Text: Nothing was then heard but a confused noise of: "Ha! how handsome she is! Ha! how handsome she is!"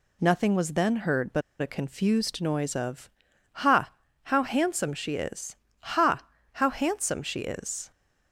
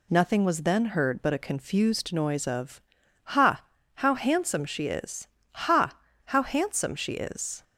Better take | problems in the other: second | pauses between "but" and "a"; slight; at 1.4 s; 0.20 s long

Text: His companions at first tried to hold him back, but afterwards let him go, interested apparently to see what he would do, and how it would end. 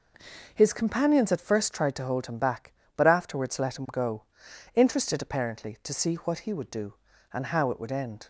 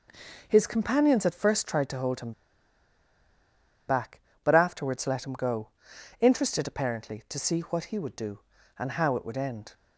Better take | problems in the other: first | pauses between "him" and "back"; strong; at 2.3 s; 1.5 s long

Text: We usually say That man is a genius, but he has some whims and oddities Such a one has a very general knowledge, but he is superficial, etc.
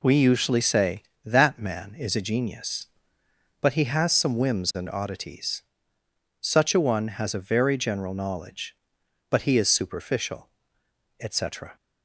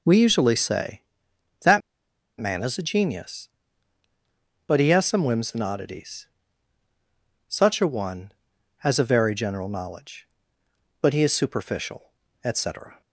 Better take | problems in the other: first | pauses between "That" and "man"; noticeable; at 1.8 s; 0.57 s long // pauses between "oddities" and "Such"; at 6.2 s; 1.2 s long; noticeable in the first

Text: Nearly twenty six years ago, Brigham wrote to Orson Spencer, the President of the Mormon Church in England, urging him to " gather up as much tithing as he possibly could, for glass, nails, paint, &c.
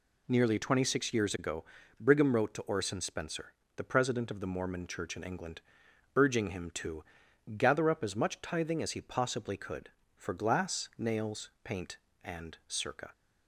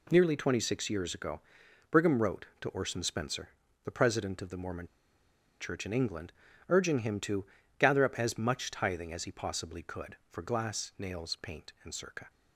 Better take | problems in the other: first | pauses between "Mormon" and "Church"; noticeable; at 4.8 s; 0.74 s long

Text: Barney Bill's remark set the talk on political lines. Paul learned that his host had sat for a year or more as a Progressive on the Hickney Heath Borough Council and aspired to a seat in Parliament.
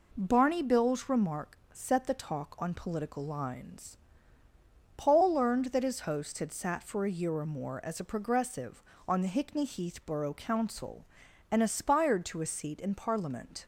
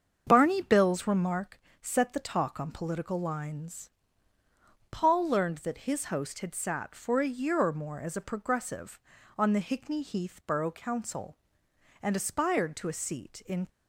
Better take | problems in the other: first | starts louder than the rest; strong; until 1.2 s; 7 dB // pauses between "remark" and "set"; slight; at 1.5 s; 0.22 s long; slight in the first // stops before "Parliament"; at 13.6 s

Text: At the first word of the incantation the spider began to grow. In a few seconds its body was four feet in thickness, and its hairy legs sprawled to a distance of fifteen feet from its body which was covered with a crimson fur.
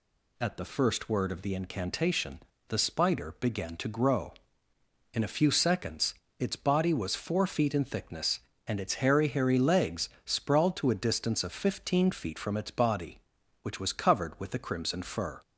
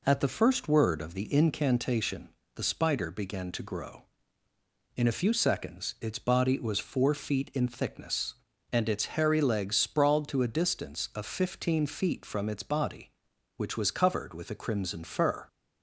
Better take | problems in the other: second | pauses between "incantation" and "the"; slight; at 2.3 s; 0.28 s long; slight in the second // pauses between "seconds" and "its"; slight; at 6.1 s; 0.26 s long // says "hairy" twice; at 9.2 s // pauses between "legs" and "sprawled"; slight; at 10.0 s; 0.16 s long

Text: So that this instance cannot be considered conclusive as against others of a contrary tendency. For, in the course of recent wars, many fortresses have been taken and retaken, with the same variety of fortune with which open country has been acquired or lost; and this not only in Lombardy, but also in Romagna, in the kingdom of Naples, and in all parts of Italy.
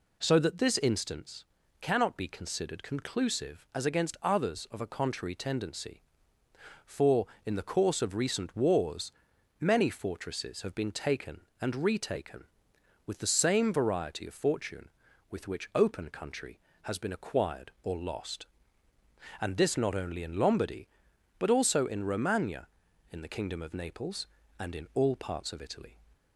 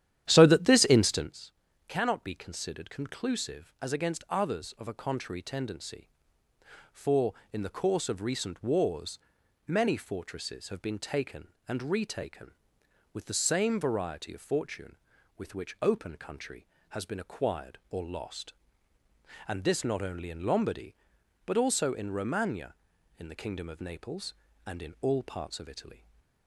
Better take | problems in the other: first | starts louder than the rest; strong; until 1.3 s; 11 dB // pauses between "instance" and "cannot"; slight; at 1.5 s; 0.36 s long; slight in the first // stays silent after the last word; slight; from 25.9 s on; 0.5 s long

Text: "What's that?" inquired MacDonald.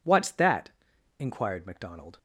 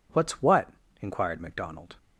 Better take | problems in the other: first | says "what" for "that"; at 0.4 s

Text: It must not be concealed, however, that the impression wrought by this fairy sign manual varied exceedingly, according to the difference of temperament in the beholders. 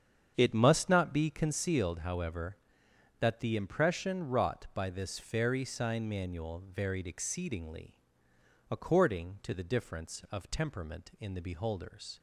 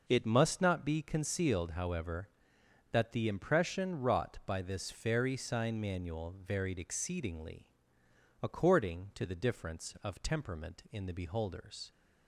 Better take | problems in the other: second | starts louder than the rest; strong; until 1.7 s; 7.5 dB

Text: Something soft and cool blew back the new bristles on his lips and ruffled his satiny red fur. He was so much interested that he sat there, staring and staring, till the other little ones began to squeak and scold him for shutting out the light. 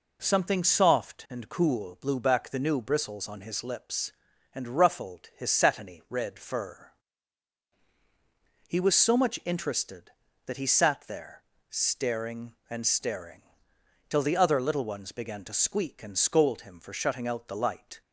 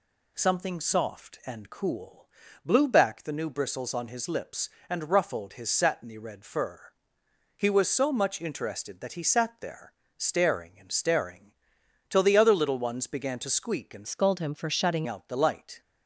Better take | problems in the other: first | pauses between "cool" and "blew"; at 2.2 s; 0.38 s long // changes voice from "scold" to "shutting"; from 14.0 to 15.0 s; 1.0 s long

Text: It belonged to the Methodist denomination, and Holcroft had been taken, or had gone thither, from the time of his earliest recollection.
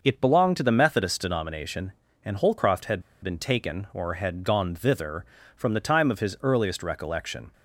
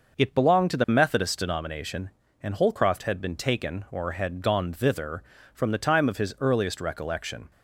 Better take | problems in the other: second | pauses between "had" and "been"; slight; at 3.0 s; 0.20 s long

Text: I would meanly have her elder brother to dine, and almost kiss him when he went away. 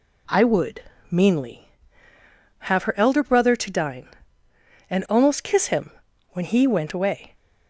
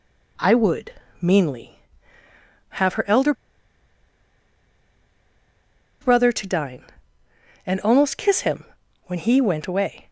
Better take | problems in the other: first | pauses between "would" and "meanly"; slight; at 0.9 s; 0.26 s long; slight in the first // pauses between "elder" and "brother"; strong; at 3.3 s; 2.6 s long // pauses between "him" and "when"; at 8.6 s; 0.42 s long; also in the first

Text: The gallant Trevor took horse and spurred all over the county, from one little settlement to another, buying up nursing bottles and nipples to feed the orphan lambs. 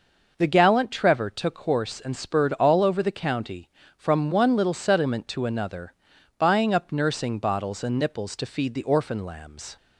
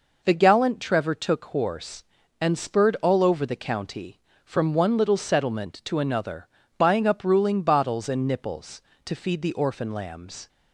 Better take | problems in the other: first | says "ruling" for "nursing"; at 7.2 s

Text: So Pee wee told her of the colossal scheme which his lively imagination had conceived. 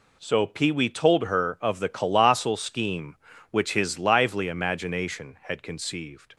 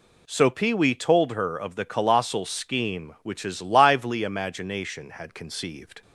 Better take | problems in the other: neither | none

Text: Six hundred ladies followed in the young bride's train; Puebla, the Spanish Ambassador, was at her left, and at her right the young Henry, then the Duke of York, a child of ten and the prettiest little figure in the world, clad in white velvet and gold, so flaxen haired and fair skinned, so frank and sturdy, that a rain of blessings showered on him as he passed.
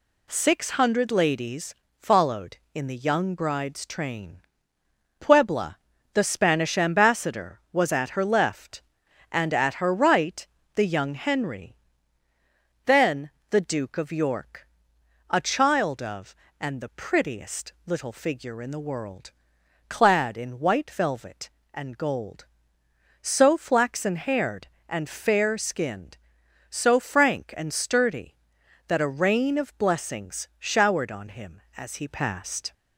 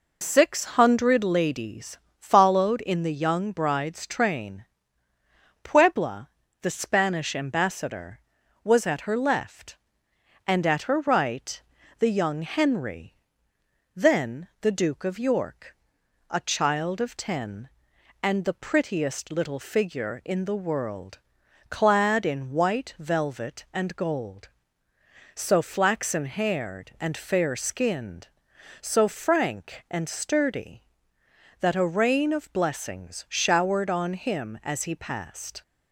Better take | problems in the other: second | pauses between "ladies" and "followed"; slight; at 1.7 s; 0.24 s long; slight in the second // pauses between "right" and "the"; slight; at 10.4 s; 0.30 s long; also in the second // pauses between "then" and "the"; slight; at 13.3 s; 0.18 s long // skips "ten"; at 16.4 s

